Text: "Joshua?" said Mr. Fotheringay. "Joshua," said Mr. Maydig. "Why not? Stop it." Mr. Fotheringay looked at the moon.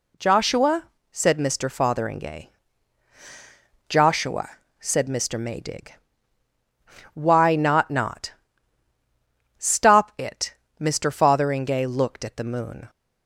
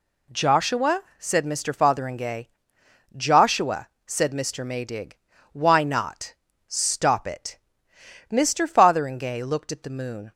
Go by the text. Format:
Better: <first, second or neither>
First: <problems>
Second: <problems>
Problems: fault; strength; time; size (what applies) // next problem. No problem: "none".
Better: second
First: says "not" twice; at 7.9 s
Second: none